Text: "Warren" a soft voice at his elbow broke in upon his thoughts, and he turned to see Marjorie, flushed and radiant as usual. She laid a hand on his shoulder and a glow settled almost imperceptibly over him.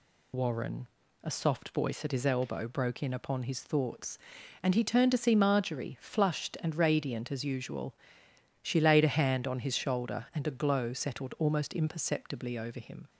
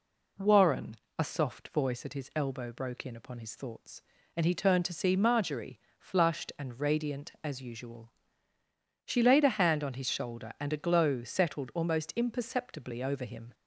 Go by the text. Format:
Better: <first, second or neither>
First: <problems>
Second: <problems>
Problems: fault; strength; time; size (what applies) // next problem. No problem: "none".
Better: second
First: loses the start of "Warren"; at 0.3 s; 80 ms // pauses between "Warren" and "a"; slight; at 0.8 s; 0.34 s long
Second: pauses between "Warren" and "a"; slight; at 0.9 s; 0.22 s long